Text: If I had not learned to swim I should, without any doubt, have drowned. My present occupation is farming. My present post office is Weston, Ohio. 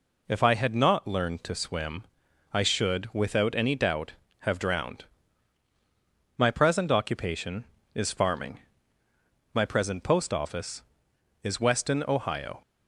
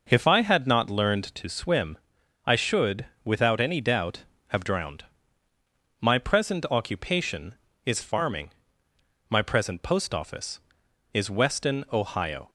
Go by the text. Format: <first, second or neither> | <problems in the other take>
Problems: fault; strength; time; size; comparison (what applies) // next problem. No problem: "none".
neither | pauses between "swim" and "I"; noticeable; the same in both